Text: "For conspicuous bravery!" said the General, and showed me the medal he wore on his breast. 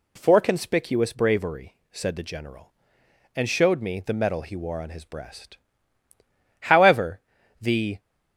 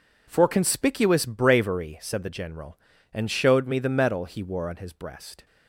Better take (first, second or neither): second